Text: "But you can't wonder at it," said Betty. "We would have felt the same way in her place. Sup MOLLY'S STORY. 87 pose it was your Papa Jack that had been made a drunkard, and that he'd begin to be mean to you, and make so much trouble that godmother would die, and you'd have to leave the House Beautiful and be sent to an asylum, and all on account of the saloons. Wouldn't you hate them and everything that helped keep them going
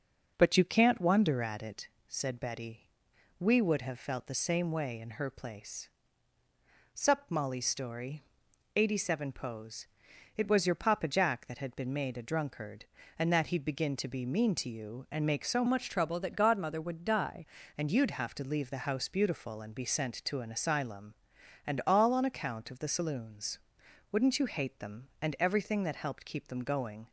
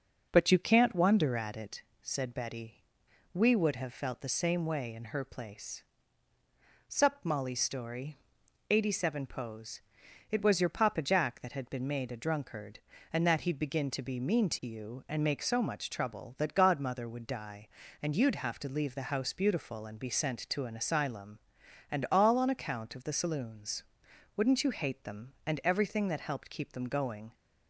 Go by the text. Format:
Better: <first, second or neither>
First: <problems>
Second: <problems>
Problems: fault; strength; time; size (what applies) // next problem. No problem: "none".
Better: second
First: starts louder than the rest; noticeable; until 1.3 s; 6 dB // pauses between "pose" and "it"; noticeable; at 9.8 s; 0.50 s long // changes voice from "much" to "die"; from 15.6 to 17.4 s; 1.8 s long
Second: starts louder than the rest; noticeable; until 1.3 s; 6 dB // pauses between "pose" and "it"; noticeable; at 9.8 s; 0.50 s long